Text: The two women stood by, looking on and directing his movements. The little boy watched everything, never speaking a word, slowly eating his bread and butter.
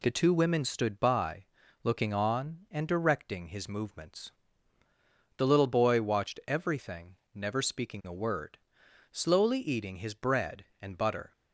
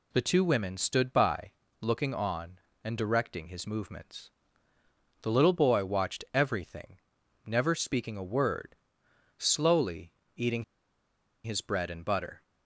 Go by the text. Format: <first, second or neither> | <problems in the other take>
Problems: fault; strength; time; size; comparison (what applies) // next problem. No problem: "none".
first | pauses between "slowly" and "eating"; slight; at 10.1 s; 0.24 s long // pauses between "eating" and "his"; noticeable; at 10.6 s; 0.80 s long